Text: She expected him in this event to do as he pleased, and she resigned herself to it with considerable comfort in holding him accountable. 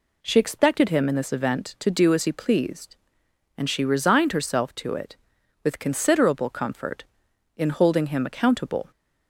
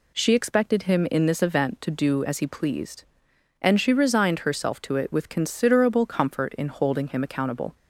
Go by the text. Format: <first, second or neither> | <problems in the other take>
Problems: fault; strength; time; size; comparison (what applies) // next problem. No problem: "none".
neither | none